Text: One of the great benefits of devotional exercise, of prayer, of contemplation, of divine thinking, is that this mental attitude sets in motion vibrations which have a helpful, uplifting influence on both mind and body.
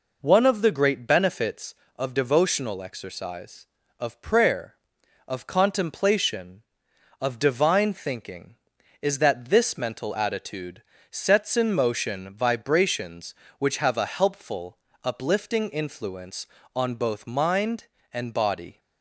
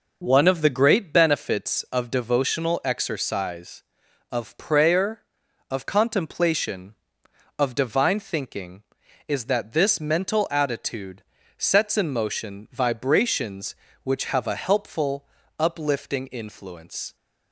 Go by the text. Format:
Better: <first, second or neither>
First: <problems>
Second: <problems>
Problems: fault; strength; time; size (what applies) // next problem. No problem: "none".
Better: first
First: pauses between "attitude" and "sets"; slight; at 10.8 s; 0.28 s long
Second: pauses between "attitude" and "sets"; slight; at 11.2 s; 0.34 s long // stops before "on both mind and body"; at 17.1 s